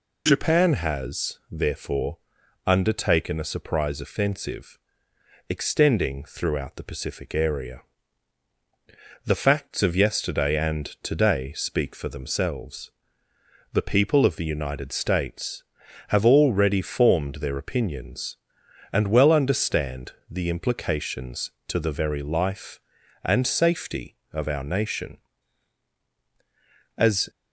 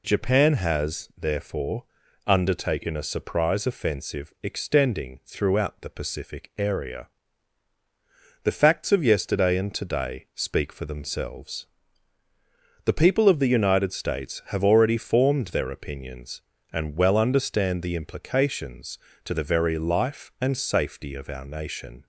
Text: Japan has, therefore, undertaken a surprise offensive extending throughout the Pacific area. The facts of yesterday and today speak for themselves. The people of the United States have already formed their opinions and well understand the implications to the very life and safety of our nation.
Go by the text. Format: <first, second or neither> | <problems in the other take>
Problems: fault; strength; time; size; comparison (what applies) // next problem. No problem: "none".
second | pauses between "offensive" and "extending"; noticeable; at 4.7 s; 0.72 s long // pauses between "and" and "today"; slight; at 10.8 s; 0.16 s long // pauses between "understand" and "the"; slight; at 20.1 s; 0.18 s long // goes on to say "As"; slight; from 26.9 s on; 0.32 s long